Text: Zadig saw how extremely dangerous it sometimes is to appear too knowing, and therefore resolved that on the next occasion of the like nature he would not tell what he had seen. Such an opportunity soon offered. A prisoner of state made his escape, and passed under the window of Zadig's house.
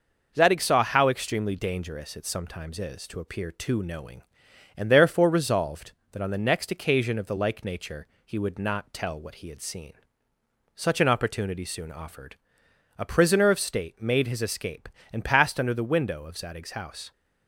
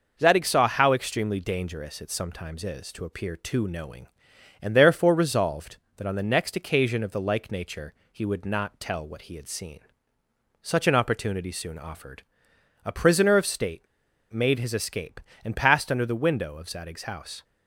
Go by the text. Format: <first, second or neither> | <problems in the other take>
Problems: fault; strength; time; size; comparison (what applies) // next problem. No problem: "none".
first | pauses between "nature" and "he"; slight; at 7.9 s; 0.20 s long; slight in the first // pauses between "state" and "made"; noticeable; at 13.8 s; 0.48 s long